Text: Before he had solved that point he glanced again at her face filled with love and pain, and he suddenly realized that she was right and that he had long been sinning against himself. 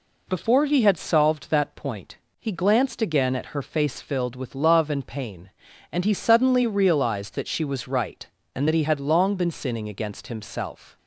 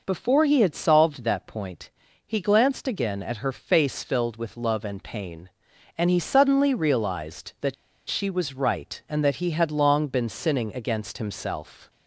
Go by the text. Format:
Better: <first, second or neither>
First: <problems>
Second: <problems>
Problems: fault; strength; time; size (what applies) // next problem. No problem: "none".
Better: first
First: pauses between "point" and "he"; slight; at 2.1 s; 0.20 s long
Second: pauses between "point" and "he"; slight; at 1.8 s; 0.36 s long // pauses between "that" and "she"; slight; at 7.7 s; 0.35 s long